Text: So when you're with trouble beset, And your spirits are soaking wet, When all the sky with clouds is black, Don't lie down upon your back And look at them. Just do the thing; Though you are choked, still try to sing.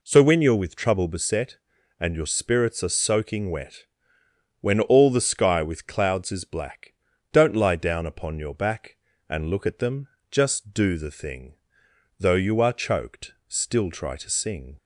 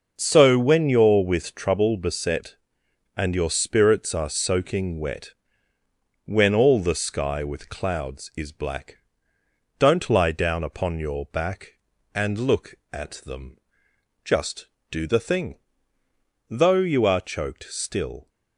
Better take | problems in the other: first | stops before "try to sing"; at 18.2 s

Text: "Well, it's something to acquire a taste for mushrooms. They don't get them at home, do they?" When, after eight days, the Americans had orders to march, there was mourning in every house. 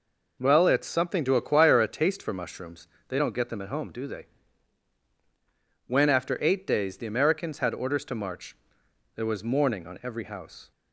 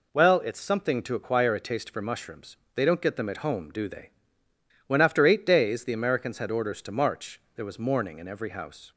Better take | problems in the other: second | says "on" for "in"; at 9.8 s

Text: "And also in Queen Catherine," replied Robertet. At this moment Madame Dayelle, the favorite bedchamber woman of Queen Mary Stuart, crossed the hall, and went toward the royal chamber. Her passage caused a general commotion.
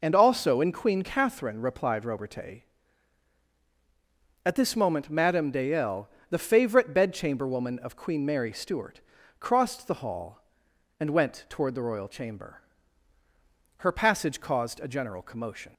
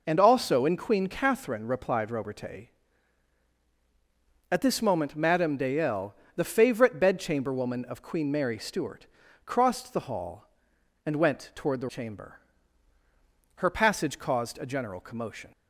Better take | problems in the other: first | skips "royal"; at 11.8 s

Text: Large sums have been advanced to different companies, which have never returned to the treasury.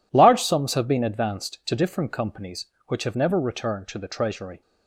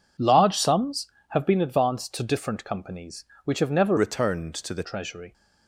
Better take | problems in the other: first | changes voice from "returned" to "the"; from 3.9 to 4.8 s; 0.9 s long

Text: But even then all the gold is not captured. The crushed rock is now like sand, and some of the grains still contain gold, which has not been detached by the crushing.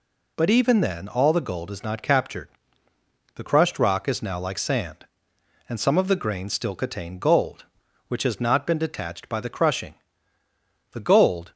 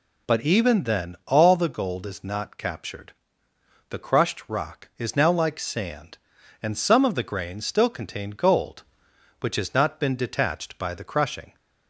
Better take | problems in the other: second | goes on to say "The gold"; from 10.9 s on; 0.60 s long

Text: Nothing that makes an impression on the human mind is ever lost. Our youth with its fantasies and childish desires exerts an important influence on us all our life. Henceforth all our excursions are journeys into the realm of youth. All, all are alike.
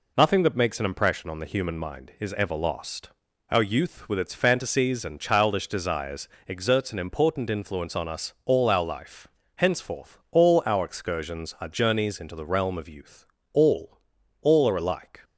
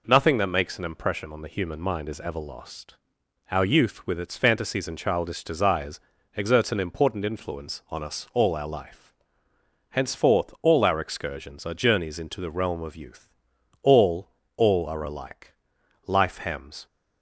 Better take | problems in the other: first | pauses between "desires" and "exerts"; slight; at 5.9 s; 0.36 s long; slight in the first // goes on to say "Life hems"; noticeable; from 16.0 s on; 0.78 s long

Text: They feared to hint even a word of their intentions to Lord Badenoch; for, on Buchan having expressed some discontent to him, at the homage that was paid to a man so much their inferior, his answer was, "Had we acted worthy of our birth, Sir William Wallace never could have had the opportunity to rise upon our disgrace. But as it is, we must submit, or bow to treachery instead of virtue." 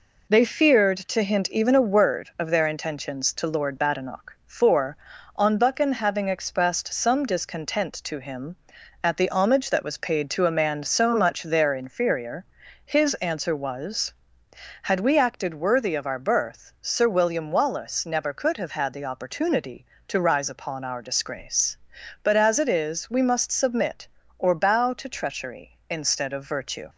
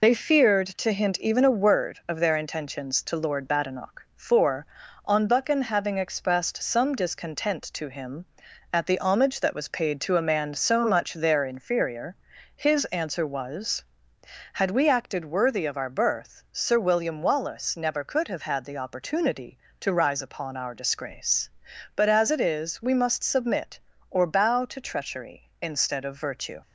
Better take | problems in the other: first | loses the start of "They"; at 0.0 s; 40 ms

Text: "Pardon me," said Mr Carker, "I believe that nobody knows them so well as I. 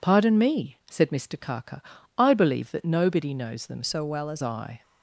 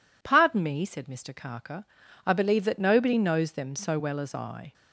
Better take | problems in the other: second | changes voice from "so" to "as"; from 3.8 to 4.4 s; 0.6 s long

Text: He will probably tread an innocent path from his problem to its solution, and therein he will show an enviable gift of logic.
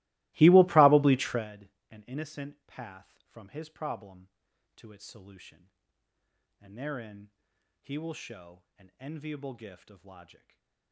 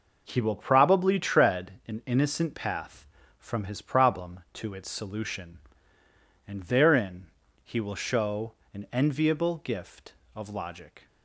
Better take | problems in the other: second | starts louder than the rest; strong; until 1.5 s; 20.5 dB // pauses between "tread" and "an"; slight; at 1.6 s; 0.22 s long; slight in the second // pauses between "therein" and "he"; noticeable; at 7.2 s; 0.50 s long; also in the second // pauses between "show" and "an"; slight; at 8.6 s; 0.16 s long; slight in the second // stays silent after the last word; slight; from 10.3 s on; 0.6 s long

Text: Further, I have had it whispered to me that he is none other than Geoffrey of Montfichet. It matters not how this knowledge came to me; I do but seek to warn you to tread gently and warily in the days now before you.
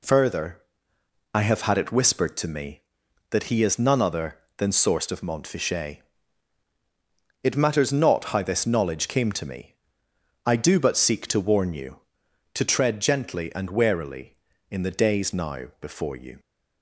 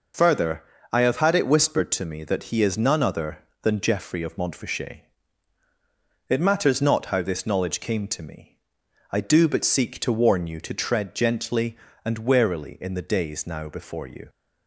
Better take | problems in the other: second | says "Sourced" for "Geoffrey"; at 4.6 s

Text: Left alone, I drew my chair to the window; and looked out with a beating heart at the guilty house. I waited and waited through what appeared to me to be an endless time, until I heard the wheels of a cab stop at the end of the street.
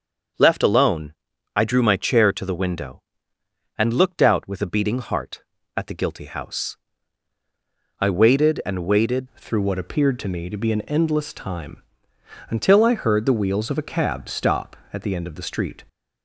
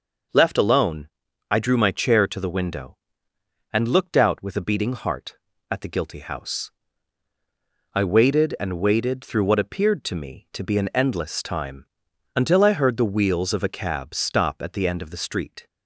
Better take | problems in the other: second | starts louder than the rest; until 1.7 s; 6.5 dB // changes voice at "through"; from 9.3 s on; 6.5 s long

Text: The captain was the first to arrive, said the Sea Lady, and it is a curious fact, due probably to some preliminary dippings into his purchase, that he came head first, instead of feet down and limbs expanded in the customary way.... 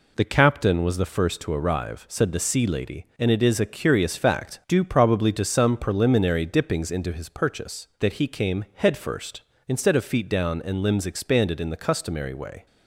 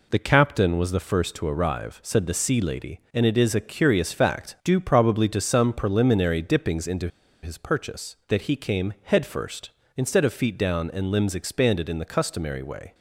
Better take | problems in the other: first | pauses between "into" and "his"; slight; at 7.0 s; 0.35 s long

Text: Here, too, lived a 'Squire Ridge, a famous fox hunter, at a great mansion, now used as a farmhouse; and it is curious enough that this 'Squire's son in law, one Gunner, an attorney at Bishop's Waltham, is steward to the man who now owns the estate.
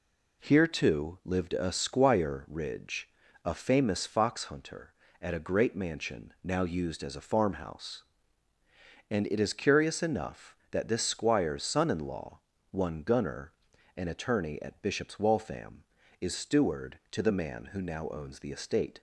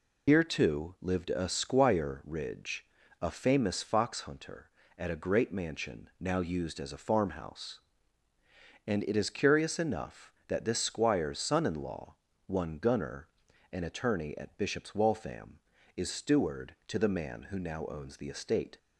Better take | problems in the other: first | loses the start of "Here"; at 0.2 s; 110 ms

